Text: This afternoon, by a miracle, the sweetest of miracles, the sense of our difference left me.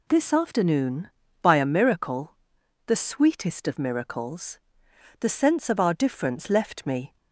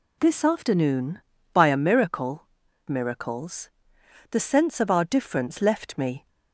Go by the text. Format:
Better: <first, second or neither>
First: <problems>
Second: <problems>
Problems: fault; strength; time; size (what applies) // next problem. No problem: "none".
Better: first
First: none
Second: skips "the sweetest of"; at 2.6 s